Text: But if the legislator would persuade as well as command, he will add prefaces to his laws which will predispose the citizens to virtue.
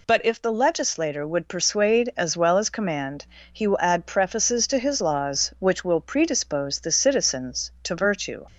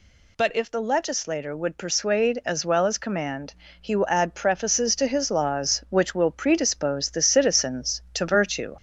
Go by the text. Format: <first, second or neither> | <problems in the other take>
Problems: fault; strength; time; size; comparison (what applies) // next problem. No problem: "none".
first | gets louder; slight; throughout; 3 dB